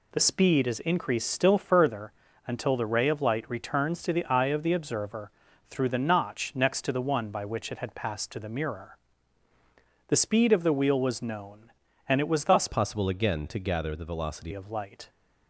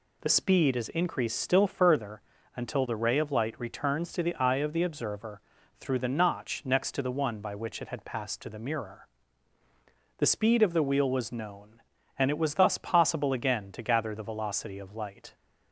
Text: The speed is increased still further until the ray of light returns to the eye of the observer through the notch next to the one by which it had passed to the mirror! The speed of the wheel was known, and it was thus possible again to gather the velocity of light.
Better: second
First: pauses between "further" and "until"; slight; at 2.1 s; 0.34 s long // pauses between "observer" and "through"; at 5.3 s; 0.38 s long // changes voice from "possible" to "velocity"; from 12.6 to 14.5 s; 1.9 s long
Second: pauses between "further" and "until"; slight; at 2.2 s; 0.34 s long // pauses between "observer" and "through"; at 5.4 s; 0.38 s long

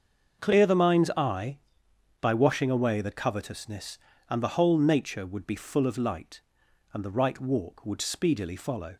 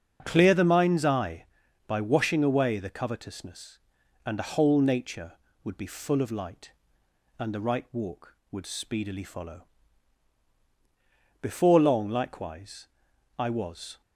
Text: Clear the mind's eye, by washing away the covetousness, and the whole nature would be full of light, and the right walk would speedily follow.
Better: first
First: starts louder than the rest; until 1.4 s; 6.5 dB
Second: starts louder than the rest; until 1.2 s; 6.5 dB // goes on to say "Before long likewise I was"; strong; from 11.4 s on; 2.6 s long

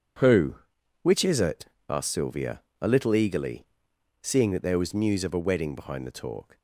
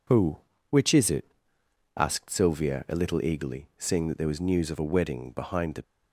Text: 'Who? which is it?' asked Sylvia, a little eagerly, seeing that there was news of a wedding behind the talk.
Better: first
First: none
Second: stops before "talk"; at 5.8 s

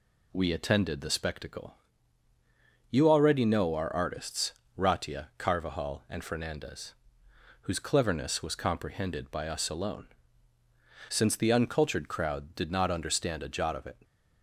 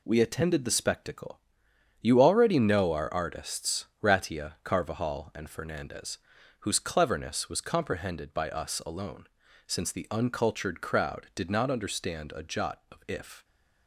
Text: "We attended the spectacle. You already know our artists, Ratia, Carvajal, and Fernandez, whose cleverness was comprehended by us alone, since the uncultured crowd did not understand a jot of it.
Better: first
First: none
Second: says "if" for "it"; at 13.0 s

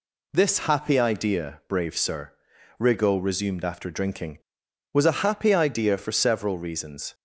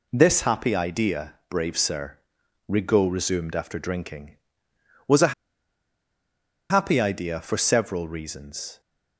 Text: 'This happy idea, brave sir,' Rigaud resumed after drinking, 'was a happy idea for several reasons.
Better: first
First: none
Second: pauses between "a" and "happy"; strong; at 5.3 s; 1.3 s long

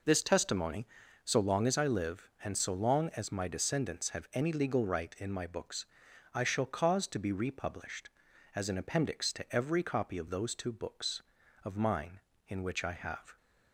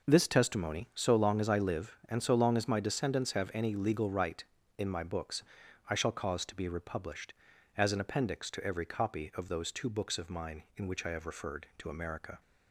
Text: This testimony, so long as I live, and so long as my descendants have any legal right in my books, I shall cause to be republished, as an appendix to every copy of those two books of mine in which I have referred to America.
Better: second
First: stops before "referred to America"; at 13.3 s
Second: none

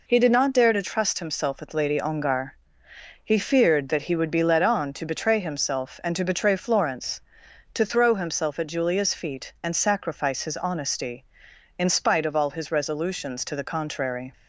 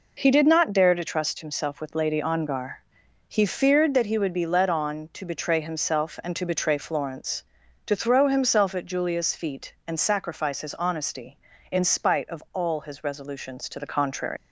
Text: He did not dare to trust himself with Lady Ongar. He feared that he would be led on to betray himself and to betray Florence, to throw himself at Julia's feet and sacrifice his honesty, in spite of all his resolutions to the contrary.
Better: first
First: none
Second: leaves "contrary" unfinished; at 14.3 s; 145 ms

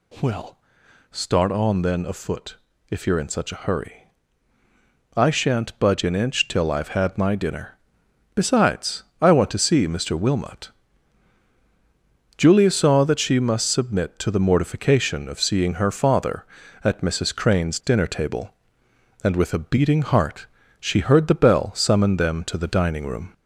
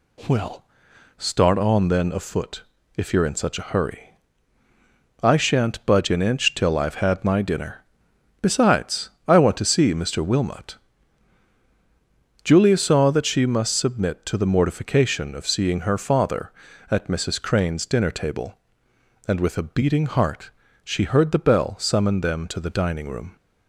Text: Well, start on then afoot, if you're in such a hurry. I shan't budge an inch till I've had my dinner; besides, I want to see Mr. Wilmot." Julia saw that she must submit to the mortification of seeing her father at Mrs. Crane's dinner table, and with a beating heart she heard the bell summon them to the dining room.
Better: second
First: gets louder; slight; throughout; 2 dB // pauses between "heart" and "she"; slight; at 20.4 s; 0.32 s long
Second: pauses between "heart" and "she"; slight; at 20.5 s; 0.32 s long

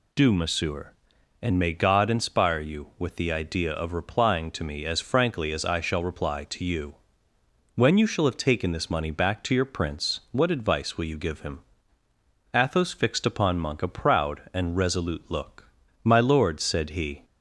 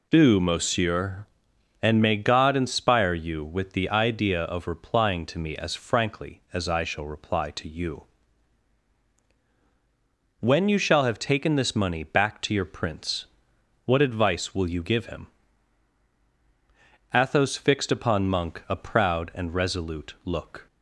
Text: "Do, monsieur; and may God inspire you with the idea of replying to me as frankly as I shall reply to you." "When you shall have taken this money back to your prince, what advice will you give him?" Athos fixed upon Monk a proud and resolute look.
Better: second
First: goes on to say "My lord said he"; noticeable; from 16.0 s on; 1.2 s long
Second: none

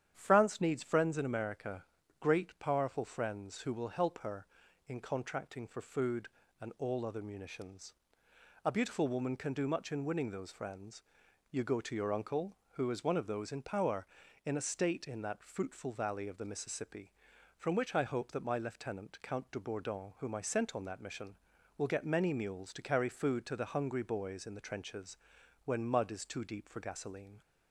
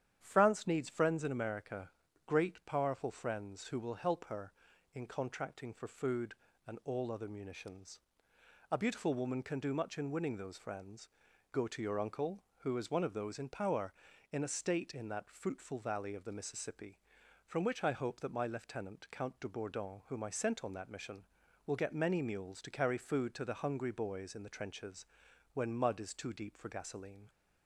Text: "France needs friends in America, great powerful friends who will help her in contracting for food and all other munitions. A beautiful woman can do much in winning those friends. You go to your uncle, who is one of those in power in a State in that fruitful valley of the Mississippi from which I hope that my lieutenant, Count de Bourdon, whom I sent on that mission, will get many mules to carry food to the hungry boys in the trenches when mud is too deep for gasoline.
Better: first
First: starts louder than the rest; strong; until 1.1 s; 9.5 dB // pauses between "trenches" and "when"; noticeable; at 25.1 s; 0.48 s long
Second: starts louder than the rest; strong; until 1.2 s; 9.5 dB // skips "You"; at 11.3 s // pauses between "trenches" and "when"; noticeable; at 25.0 s; 0.48 s long

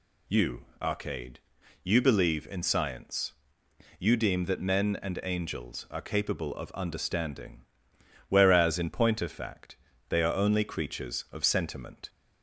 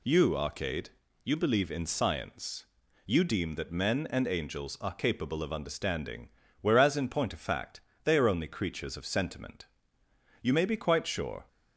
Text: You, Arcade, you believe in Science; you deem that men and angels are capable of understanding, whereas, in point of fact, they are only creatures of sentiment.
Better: first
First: none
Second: goes on to say "You may be quite sure"; noticeable; from 10.4 s on; 1.0 s long

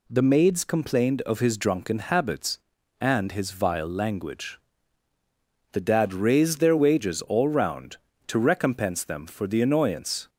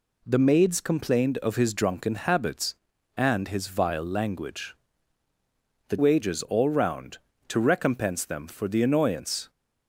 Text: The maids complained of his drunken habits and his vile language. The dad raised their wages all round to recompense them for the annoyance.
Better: first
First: none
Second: skips "dad raised their"; at 5.9 s

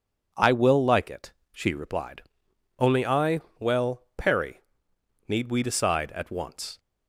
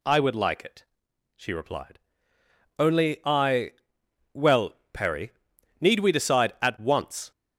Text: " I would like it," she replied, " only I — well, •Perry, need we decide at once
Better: second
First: says "will" for "would"; at 0.5 s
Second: none

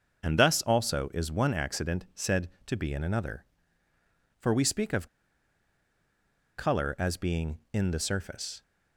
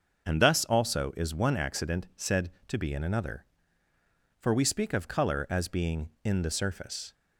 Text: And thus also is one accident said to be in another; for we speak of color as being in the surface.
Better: second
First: starts louder than the rest; until 1.3 s; 6.5 dB // pauses between "of" and "color"; strong; at 5.0 s; 1.5 s long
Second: starts louder than the rest; until 1.3 s; 6.5 dB

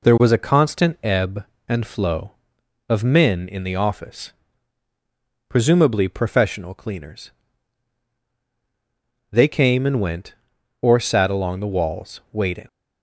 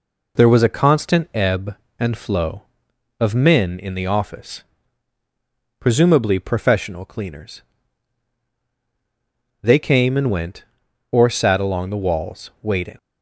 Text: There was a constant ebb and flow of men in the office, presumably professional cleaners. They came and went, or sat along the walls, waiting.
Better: neither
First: none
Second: none

